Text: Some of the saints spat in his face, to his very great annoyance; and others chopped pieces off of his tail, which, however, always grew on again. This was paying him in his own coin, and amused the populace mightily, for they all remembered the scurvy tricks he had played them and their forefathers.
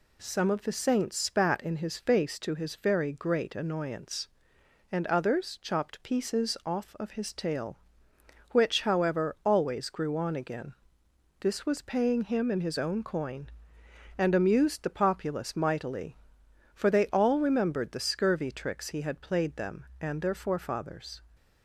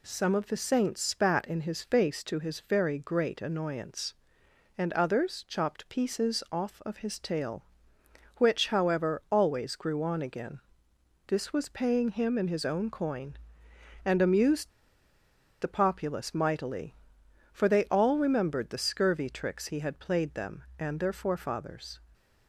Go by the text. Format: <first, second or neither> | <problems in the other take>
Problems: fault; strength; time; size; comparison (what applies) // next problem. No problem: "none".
first | pauses between "amused" and "the"; noticeable; at 14.6 s; 0.92 s long